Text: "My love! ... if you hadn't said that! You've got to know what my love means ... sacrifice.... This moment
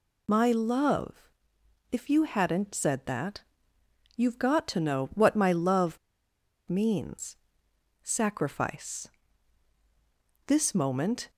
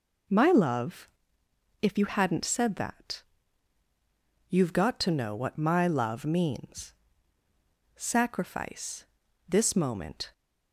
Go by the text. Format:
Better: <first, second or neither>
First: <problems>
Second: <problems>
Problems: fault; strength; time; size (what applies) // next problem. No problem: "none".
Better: second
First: pauses between "love" and "means"; noticeable; at 5.9 s; 0.69 s long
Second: none